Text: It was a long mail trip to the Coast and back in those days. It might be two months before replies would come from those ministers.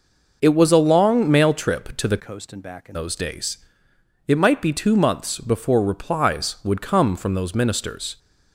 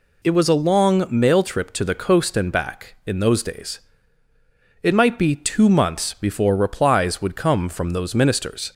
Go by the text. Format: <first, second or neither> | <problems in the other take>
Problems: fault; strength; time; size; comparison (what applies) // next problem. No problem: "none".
second | changes voice from "Coast" to "in"; from 2.1 to 2.9 s; 0.8 s long